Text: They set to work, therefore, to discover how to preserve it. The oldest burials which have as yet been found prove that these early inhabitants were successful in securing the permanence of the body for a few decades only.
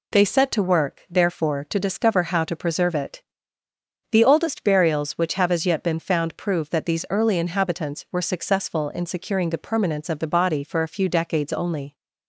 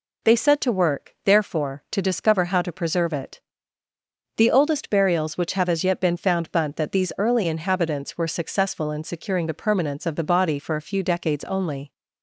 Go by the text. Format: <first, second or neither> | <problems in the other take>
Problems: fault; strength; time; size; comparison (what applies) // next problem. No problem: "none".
first | says "bunt" for "prove"; at 6.5 s